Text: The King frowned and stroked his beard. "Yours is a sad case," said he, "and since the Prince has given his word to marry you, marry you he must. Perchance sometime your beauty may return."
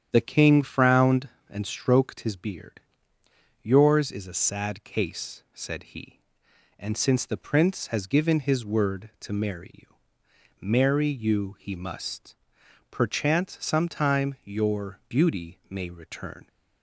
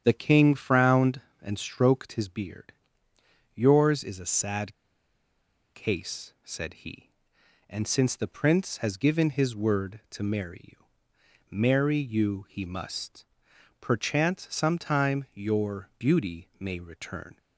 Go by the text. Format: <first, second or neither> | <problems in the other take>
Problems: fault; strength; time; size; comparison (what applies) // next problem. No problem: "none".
first | starts louder than the rest; strong; until 1.0 s; 9.5 dB; strong in the first // pauses between "sad" and "case"; at 4.7 s; 1.0 s long